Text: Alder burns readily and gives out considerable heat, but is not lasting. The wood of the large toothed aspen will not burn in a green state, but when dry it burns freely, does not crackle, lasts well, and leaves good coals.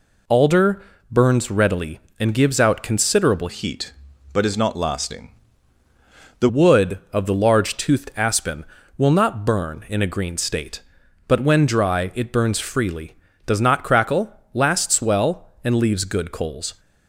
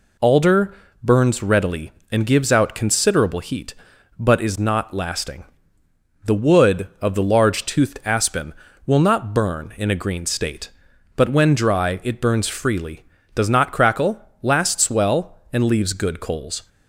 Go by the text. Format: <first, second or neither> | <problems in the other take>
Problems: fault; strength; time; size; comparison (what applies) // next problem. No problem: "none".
second | pauses between "Alder" and "burns"; slight; at 0.8 s; 0.30 s long; slight in the second // changes voice from "heat" to "The"; from 3.4 to 6.4 s; 3.0 s long